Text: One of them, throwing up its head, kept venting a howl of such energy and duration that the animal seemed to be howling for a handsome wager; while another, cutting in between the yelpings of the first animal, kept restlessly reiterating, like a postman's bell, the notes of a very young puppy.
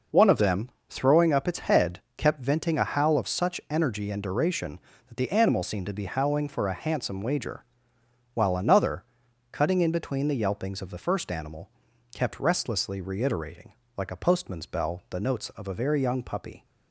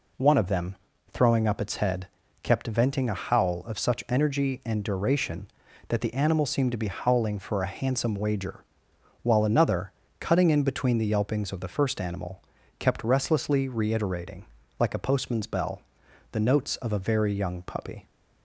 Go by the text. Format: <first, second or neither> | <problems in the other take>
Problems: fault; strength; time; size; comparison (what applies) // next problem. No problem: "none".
neither | none